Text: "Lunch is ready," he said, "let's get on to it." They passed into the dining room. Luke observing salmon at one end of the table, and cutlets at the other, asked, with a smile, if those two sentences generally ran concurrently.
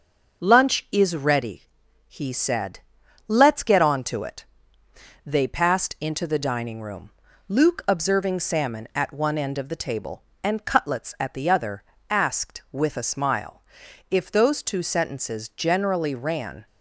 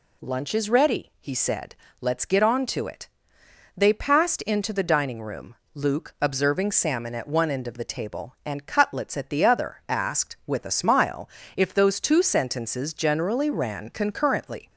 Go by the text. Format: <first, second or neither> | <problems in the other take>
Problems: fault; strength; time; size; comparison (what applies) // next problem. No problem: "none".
second | starts louder than the rest; noticeable; until 1.4 s; 6 dB // stops before "concurrently"; at 16.6 s